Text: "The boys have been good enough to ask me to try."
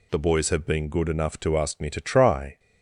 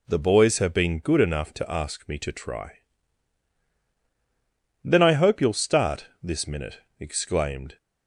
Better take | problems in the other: first | goes on to say "Then I hope you'll start this minute exclaimed"; strong; from 4.8 s on; 2.9 s long

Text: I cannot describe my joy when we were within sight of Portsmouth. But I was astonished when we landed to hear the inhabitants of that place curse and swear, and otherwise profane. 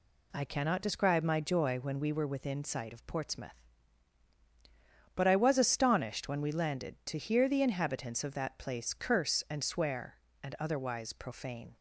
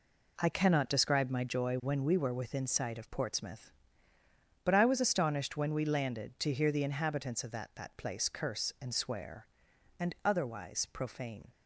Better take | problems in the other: first | says "that" twice; at 7.7 s

